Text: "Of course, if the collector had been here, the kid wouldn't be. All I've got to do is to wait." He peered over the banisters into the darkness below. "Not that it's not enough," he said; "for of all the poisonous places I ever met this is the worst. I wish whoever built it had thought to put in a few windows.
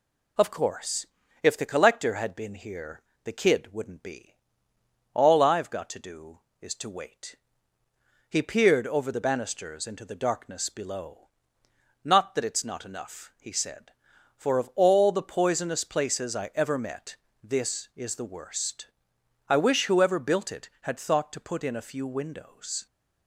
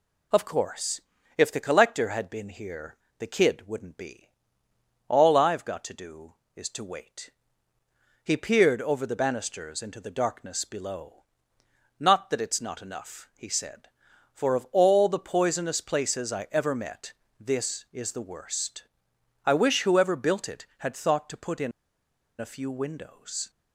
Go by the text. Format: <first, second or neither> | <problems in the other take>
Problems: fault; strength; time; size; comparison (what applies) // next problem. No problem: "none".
first | pauses between "met" and "this"; slight; at 17.1 s; 0.26 s long; slight in the first // pauses between "in" and "a"; noticeable; at 21.7 s; 0.68 s long